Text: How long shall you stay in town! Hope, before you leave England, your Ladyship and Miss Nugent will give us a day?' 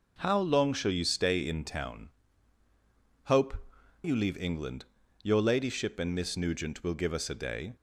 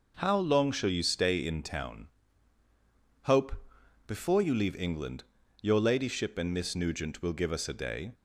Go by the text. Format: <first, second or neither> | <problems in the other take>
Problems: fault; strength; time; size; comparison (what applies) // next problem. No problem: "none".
second | skips "before"; at 3.7 s